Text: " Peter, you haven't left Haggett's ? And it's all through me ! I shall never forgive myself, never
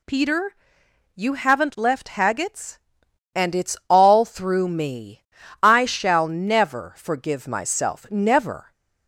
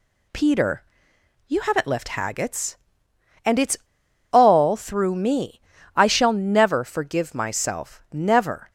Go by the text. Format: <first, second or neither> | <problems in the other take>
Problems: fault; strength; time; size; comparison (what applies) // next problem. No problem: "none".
first | pauses between "it's" and "all"; noticeable; at 3.7 s; 0.53 s long